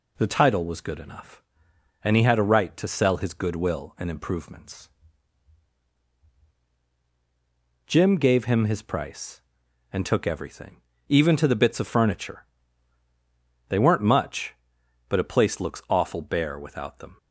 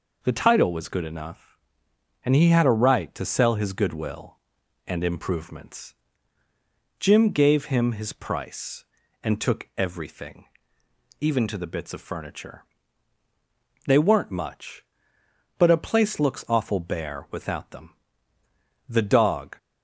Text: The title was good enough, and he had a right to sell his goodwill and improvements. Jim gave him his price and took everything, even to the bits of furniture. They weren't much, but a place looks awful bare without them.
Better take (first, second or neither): first